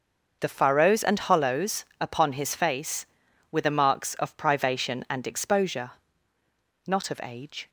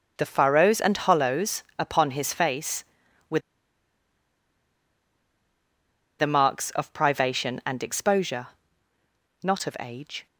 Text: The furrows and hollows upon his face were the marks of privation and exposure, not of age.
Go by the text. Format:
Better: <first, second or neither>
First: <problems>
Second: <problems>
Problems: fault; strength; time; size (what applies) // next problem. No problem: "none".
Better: first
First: starts louder than the rest; until 1.4 s; 6 dB // pauses between "hollows" and "upon"; slight; at 1.8 s; 0.16 s long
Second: starts louder than the rest; until 1.1 s; 6 dB // pauses between "hollows" and "upon"; slight; at 1.6 s; 0.16 s long // pauses between "were" and "the"; strong; at 3.3 s; 2.8 s long